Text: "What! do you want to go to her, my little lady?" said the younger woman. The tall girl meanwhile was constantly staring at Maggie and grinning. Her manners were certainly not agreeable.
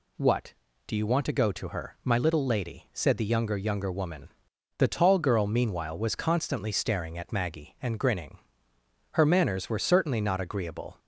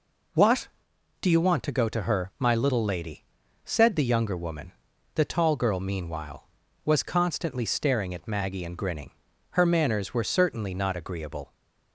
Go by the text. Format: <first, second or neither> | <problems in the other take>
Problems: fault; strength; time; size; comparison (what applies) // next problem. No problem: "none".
second | says "younger" twice; at 3.5 s